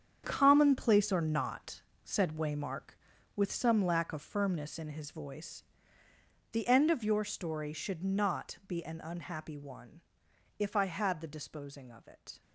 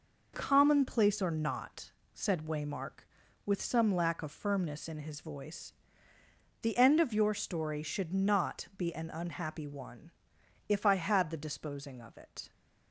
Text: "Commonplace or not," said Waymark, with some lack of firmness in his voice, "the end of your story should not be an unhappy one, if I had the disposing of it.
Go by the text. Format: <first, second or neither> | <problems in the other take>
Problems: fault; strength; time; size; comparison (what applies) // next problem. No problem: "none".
second | gets quieter; strong; throughout; 11.5 dB